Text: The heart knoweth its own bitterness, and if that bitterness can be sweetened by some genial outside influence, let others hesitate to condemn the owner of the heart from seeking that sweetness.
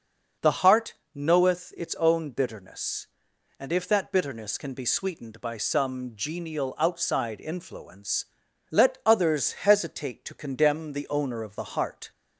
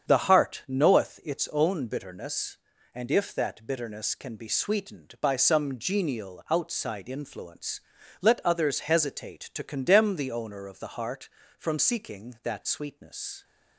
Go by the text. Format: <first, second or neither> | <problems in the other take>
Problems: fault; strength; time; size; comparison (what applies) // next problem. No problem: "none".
second | starts louder than the rest; until 1.6 s; 6.5 dB; strong in the second // pauses between "heart" and "knoweth"; slight; at 0.9 s; 0.22 s long // stops before "from seeking that sweetness"; at 12.1 s